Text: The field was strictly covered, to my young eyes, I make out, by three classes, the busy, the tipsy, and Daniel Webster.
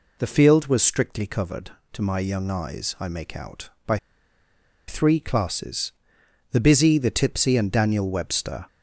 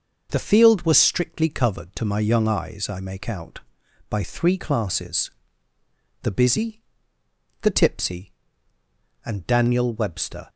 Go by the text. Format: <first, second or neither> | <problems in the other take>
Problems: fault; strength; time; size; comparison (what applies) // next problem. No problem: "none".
second | pauses between "by" and "three"; noticeable; at 3.9 s; 0.89 s long